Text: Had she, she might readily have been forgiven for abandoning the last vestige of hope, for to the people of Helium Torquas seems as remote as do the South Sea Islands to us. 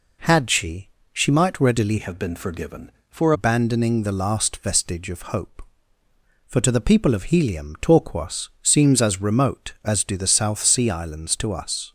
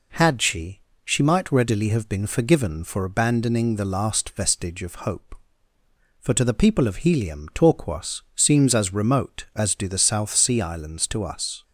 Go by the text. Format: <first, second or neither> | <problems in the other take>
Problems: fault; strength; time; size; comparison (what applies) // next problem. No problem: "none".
second | changes voice from "have" to "for"; from 1.9 to 3.3 s; 1.4 s long